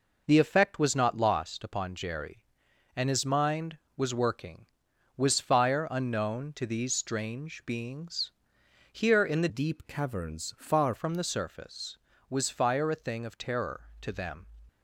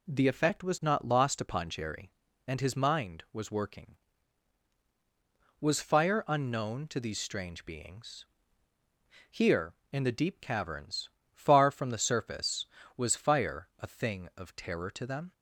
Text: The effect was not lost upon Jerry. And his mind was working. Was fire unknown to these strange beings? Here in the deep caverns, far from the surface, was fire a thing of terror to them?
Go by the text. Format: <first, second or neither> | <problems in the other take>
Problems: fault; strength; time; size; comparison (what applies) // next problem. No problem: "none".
second | changes voice from "deep" to "far"; from 9.4 to 10.9 s; 1.5 s long